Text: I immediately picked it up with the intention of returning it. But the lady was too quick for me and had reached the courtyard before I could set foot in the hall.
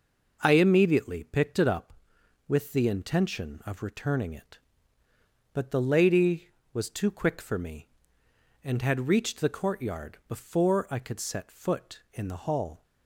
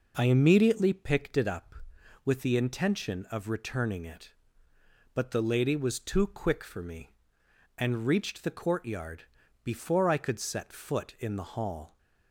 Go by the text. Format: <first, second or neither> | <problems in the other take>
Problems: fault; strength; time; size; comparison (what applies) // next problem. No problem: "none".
first | skips "had"; at 8.0 s // pauses between "courtyard" and "before"; at 9.2 s; 0.40 s long